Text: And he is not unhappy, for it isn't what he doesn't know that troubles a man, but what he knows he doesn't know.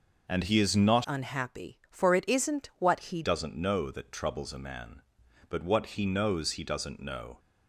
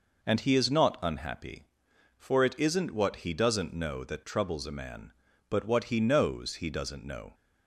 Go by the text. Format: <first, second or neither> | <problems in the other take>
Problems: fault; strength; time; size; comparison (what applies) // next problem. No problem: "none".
second | changes voice from "unhappy" to "he"; from 1.0 to 3.2 s; 2.2 s long